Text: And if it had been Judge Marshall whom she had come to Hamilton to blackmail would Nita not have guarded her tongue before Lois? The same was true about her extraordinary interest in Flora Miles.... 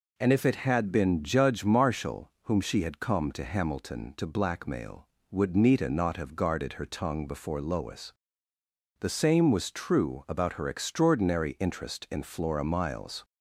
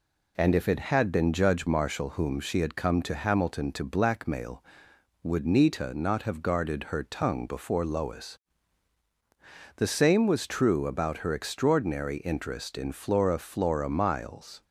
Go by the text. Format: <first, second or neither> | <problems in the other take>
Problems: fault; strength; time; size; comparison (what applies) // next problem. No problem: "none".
first | says "Flora" twice; at 13.3 s